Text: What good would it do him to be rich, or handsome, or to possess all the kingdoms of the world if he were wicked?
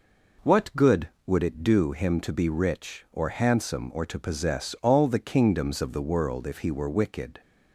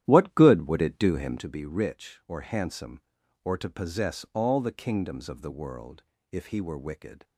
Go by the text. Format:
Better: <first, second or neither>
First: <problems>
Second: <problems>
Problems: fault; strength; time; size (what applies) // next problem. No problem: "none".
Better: first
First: none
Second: starts louder than the rest; strong; until 1.6 s; 12 dB // pauses between "world" and "if"; slight; at 6.0 s; 0.26 s long